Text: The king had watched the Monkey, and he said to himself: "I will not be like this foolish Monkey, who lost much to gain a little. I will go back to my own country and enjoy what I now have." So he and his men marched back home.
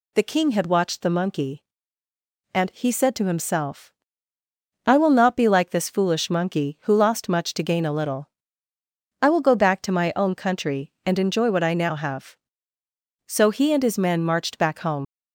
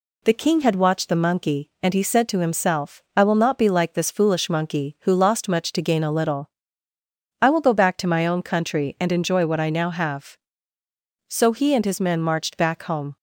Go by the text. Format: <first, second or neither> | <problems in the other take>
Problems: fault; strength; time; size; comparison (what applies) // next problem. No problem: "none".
second | leaves "home" unfinished; at 15.0 s; 80 ms